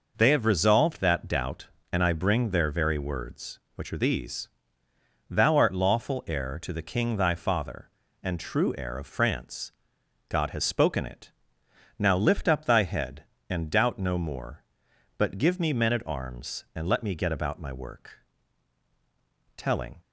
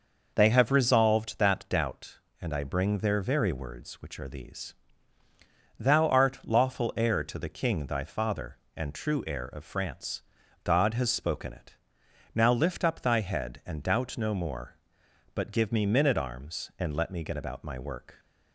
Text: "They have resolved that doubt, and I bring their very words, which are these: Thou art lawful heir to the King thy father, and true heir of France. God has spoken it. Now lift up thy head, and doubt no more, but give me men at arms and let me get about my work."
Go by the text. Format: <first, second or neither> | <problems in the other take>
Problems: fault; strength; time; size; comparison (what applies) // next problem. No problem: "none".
second | goes on to say "Telling"; slight; from 19.5 s on; 0.42 s long